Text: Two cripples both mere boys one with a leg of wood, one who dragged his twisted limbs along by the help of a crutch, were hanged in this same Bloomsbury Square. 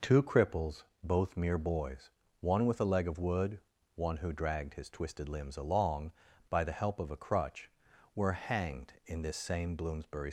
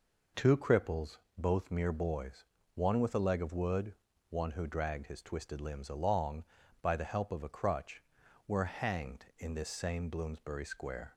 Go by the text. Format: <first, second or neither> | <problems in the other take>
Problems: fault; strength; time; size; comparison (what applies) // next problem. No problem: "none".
second | pauses between "cripples" and "both"; slight; at 0.8 s; 0.22 s long; slight in the second // pauses between "boys" and "one"; slight; at 2.0 s; 0.30 s long; slight in the second // stops before "Square"; at 10.2 s